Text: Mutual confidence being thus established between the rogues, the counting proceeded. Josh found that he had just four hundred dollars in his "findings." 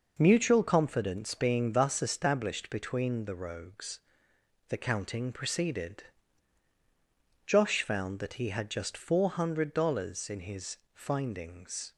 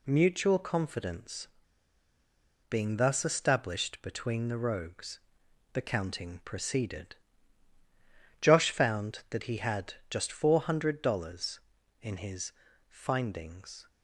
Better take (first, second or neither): first